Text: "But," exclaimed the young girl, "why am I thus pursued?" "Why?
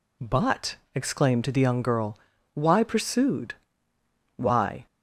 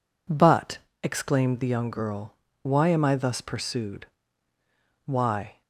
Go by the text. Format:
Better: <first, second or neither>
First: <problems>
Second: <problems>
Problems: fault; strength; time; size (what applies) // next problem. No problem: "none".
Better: second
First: skips "am I thus"; at 2.8 s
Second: none